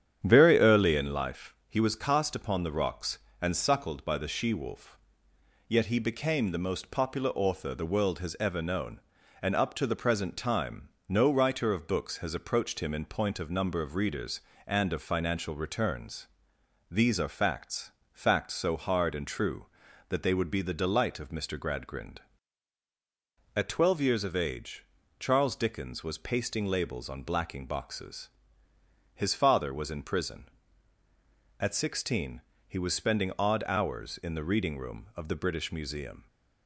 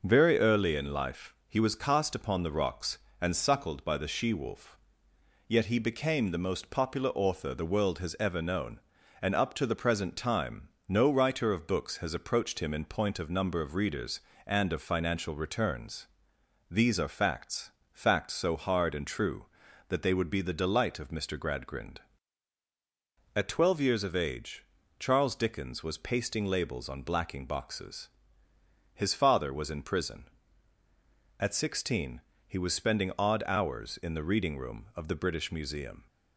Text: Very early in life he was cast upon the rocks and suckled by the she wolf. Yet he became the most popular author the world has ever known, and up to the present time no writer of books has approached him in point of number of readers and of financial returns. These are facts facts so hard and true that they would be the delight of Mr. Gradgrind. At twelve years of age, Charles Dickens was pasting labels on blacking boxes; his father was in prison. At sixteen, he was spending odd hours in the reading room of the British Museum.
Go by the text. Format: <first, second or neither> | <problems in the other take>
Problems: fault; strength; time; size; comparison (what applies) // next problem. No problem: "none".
second | starts louder than the rest; strong; until 1.2 s; 9 dB // pauses between "time" and "no"; slight; at 10.8 s; 0.18 s long; slight in the second // pauses between "facts" and "facts"; slight; at 17.8 s; 0.24 s long; slight in the second